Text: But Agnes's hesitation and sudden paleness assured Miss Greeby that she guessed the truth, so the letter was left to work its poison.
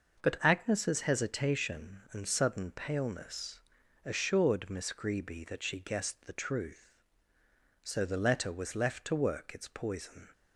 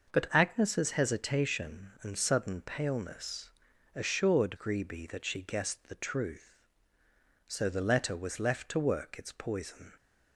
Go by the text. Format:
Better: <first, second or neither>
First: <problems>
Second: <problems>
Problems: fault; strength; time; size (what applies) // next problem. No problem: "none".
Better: first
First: pauses between "paleness" and "assured"; at 3.6 s; 0.44 s long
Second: pauses between "paleness" and "assured"; at 3.5 s; 0.44 s long // skips "Miss"; at 4.5 s